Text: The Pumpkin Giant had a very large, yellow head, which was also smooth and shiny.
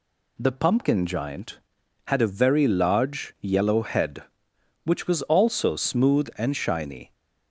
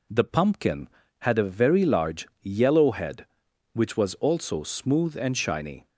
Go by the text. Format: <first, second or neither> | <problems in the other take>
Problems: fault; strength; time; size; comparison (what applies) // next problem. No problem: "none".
first | skips "Giant"; at 1.0 s